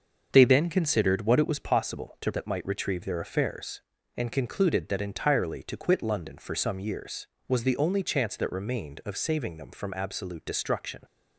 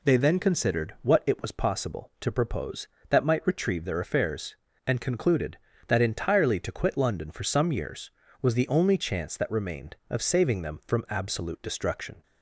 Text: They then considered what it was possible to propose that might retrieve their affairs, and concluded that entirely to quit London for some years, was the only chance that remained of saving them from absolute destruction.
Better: second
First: starts louder than the rest; until 1.3 s; 6.5 dB // skips "propose"; at 2.3 s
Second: none

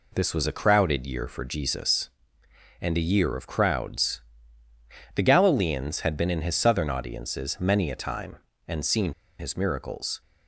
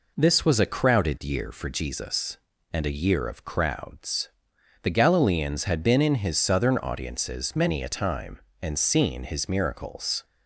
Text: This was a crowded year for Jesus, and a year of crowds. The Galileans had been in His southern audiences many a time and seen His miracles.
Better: second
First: pauses between "seen" and "His"; slight; at 9.1 s; 0.26 s long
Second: none

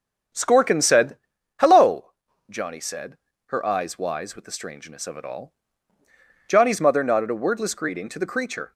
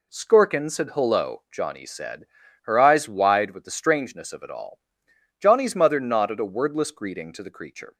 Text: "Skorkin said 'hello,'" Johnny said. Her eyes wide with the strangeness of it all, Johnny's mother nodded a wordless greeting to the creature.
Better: second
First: starts louder than the rest; strong; until 1.7 s; 7.5 dB // pauses between "said" and "hello"; at 1.1 s; 0.42 s long // says "wise" for "wide"; at 3.9 s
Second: none

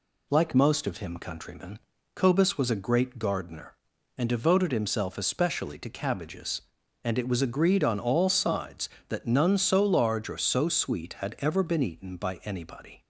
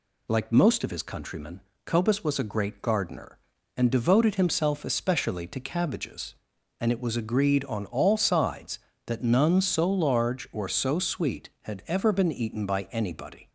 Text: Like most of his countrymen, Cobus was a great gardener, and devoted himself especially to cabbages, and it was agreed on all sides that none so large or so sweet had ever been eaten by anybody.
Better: second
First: says "him" for "his"; at 0.9 s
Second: none

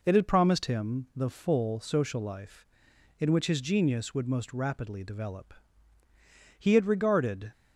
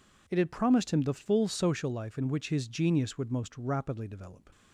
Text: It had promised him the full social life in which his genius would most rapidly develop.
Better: second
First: goes on to say "He had regarded"; noticeable; from 6.5 s on; 0.94 s long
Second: none

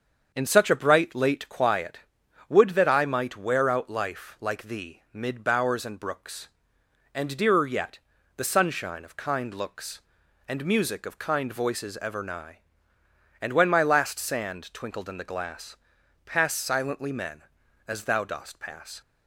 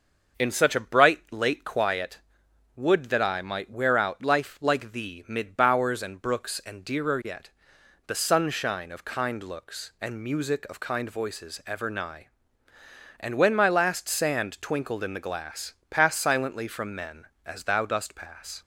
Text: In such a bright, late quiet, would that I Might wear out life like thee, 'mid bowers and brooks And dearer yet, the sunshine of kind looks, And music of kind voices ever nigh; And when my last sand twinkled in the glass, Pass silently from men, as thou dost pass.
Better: second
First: starts louder than the rest; until 1.3 s; 7 dB // skips "from"; at 17.1 s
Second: starts louder than the rest; until 1.4 s; 6.5 dB

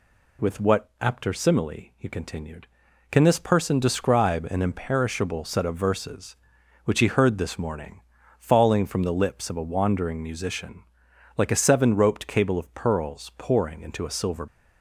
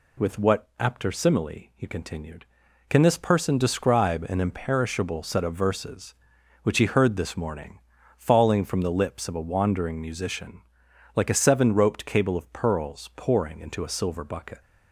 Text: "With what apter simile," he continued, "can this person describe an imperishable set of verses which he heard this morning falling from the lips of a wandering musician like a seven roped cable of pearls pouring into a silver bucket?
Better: second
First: pauses between "morning" and "falling"; at 7.9 s; 0.38 s long // pauses between "musician" and "like"; noticeable; at 10.8 s; 0.52 s long // stops before "bucket"; at 14.4 s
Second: pauses between "morning" and "falling"; at 7.7 s; 0.38 s long // pauses between "musician" and "like"; noticeable; at 10.6 s; 0.52 s long

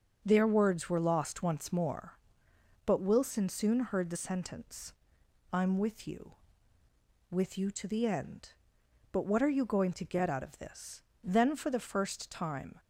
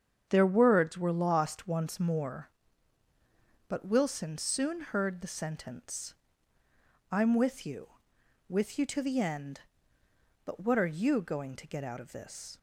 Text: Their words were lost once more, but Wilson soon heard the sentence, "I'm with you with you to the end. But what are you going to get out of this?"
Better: second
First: starts louder than the rest; until 1.2 s; 7 dB // goes on to say "Then for the first time"; from 11.2 s on; 1.5 s long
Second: starts louder than the rest; strong; until 1.3 s; 7.5 dB

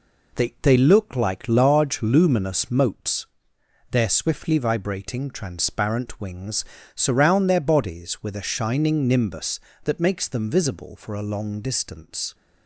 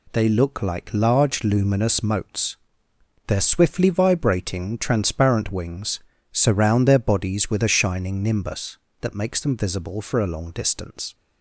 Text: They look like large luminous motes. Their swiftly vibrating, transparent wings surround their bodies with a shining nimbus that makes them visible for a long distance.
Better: second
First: says "They" twice; at 0.6 s // pauses between "wings" and "surround"; slight; at 6.6 s; 0.32 s long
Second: pauses between "wings" and "surround"; slight; at 6.0 s; 0.32 s long

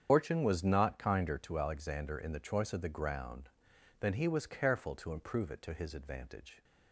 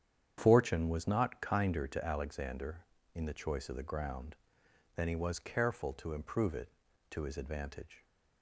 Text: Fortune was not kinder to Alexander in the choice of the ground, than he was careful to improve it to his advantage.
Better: second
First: loses the start of "Fortune"; at 0.0 s; 95 ms // starts louder than the rest; strong; until 1.1 s; 8 dB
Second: starts louder than the rest; strong; until 1.3 s; 9 dB

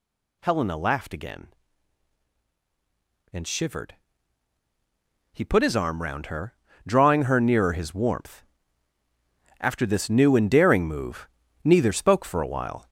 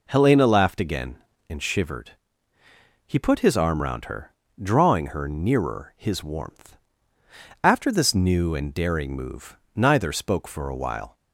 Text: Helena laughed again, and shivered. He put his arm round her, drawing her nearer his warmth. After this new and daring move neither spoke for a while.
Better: second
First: gets louder; noticeable; throughout; 5 dB // pauses between "move" and "neither"; slight; at 11.2 s; 0.36 s long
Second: pauses between "move" and "neither"; slight; at 9.5 s; 0.18 s long

